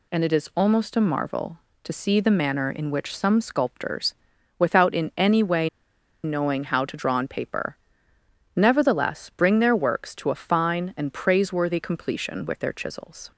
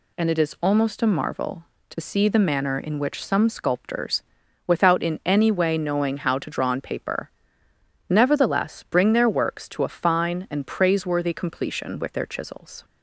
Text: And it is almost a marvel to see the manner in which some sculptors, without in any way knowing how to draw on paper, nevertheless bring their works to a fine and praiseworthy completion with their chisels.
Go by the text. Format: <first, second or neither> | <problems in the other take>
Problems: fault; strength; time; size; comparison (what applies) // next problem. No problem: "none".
second | pauses between "way" and "knowing"; noticeable; at 5.6 s; 0.55 s long